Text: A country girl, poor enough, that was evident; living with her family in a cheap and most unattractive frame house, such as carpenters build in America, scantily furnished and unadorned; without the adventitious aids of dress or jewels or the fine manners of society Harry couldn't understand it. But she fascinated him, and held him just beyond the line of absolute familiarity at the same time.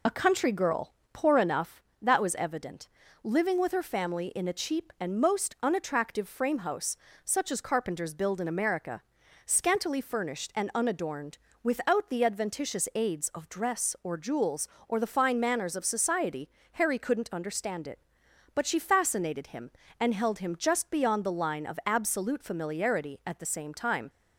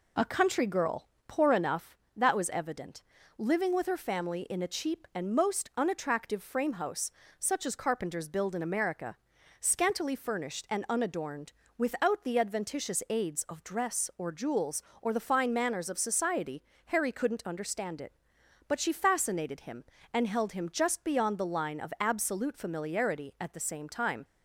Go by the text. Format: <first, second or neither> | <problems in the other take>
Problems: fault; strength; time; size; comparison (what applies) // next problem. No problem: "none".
second | loses the start of "A"; at 0.0 s; 35 ms // pauses between "society" and "Harry"; slight; at 16.4 s; 0.24 s long; slight in the second